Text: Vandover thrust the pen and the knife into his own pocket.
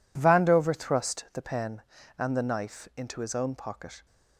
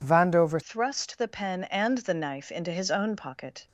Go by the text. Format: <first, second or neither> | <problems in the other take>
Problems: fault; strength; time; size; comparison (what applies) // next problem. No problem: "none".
first | changes voice at "thrust"; from 0.6 s on; 3.0 s long